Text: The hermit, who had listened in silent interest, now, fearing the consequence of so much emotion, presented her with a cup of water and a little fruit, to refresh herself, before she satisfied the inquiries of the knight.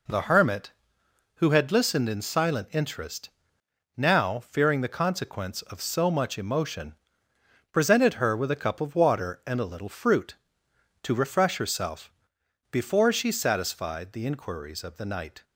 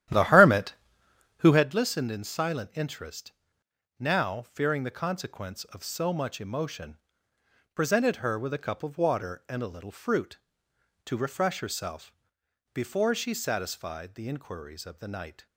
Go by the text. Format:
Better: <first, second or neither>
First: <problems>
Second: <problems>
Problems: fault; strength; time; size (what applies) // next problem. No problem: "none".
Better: first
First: none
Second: starts louder than the rest; strong; until 1.6 s; 12 dB